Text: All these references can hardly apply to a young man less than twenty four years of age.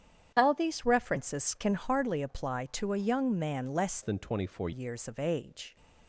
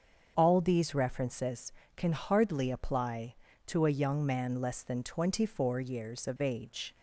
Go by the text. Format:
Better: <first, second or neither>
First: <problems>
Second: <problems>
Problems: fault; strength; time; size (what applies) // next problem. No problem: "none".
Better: second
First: starts louder than the rest; strong; until 1.3 s; 9.5 dB // changes voice from "than" to "four"; from 4.0 to 4.7 s; 0.7 s long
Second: starts louder than the rest; strong; until 1.3 s; 7.5 dB